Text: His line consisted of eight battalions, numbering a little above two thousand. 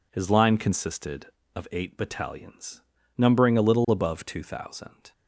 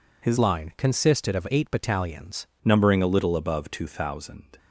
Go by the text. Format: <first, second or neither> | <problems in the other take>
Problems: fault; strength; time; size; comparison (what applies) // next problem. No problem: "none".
first | changes voice from "line" to "battalions"; from 0.3 to 2.4 s; 2.1 s long